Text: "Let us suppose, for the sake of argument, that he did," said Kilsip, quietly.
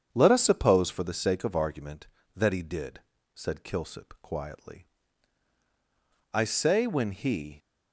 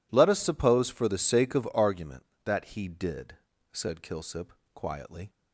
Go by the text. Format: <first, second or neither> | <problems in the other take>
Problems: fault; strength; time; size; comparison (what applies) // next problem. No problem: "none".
second | starts louder than the rest; strong; until 1.1 s; 7.5 dB // goes on to say "I say when he"; noticeable; from 6.3 s on; 1.2 s long